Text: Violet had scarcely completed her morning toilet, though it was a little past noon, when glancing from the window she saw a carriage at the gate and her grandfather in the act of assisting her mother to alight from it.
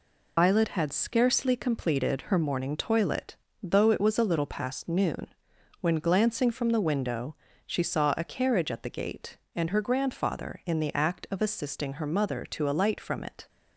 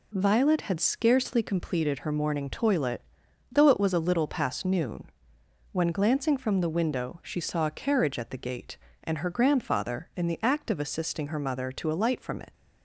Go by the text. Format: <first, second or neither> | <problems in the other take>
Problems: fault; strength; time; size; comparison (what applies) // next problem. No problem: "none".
second | loses the start of "Violet"; at 0.3 s; 75 ms // pauses between "window" and "she"; slight; at 7.3 s; 0.32 s long